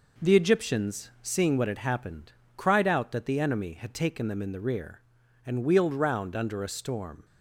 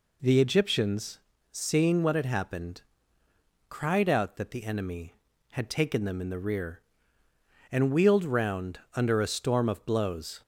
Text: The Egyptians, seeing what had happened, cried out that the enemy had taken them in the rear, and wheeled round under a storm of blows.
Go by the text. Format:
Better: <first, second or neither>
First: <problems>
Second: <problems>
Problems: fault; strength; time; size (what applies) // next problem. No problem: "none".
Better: second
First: stops before "of blows"; at 7.2 s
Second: none